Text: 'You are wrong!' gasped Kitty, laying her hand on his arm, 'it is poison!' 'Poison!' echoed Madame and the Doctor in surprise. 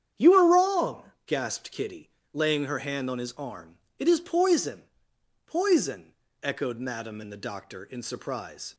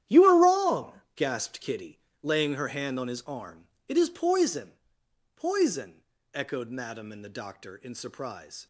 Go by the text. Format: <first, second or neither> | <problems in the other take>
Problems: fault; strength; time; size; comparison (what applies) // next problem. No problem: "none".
first | gets quieter; strong; throughout; 13 dB // starts louder than the rest; strong; until 1.2 s; 11.5 dB; strong in the first